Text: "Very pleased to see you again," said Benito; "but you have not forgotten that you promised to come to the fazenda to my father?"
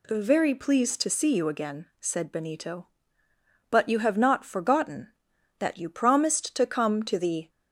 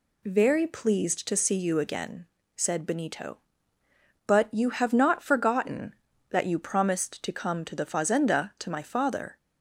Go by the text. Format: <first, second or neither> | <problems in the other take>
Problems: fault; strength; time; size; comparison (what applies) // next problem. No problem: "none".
second | stops before "fazenda to my father"; at 7.4 s